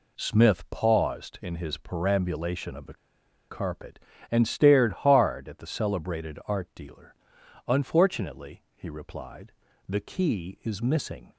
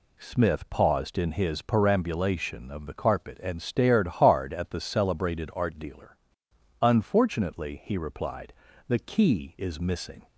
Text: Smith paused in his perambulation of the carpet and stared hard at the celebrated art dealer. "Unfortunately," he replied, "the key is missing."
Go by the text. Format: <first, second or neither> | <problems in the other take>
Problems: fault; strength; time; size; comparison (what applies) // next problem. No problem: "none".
second | pauses between "the" and "carpet"; noticeable; at 2.9 s; 0.54 s long